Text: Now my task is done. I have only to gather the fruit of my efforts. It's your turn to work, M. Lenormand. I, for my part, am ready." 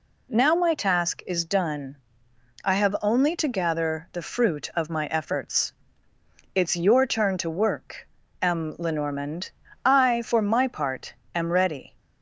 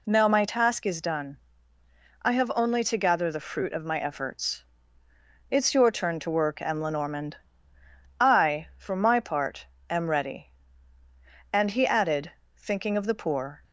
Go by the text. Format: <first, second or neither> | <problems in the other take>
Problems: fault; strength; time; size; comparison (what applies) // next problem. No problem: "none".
first | goes on to say "And he added thinking of the poor"; strong; from 11.5 s on; 2.1 s long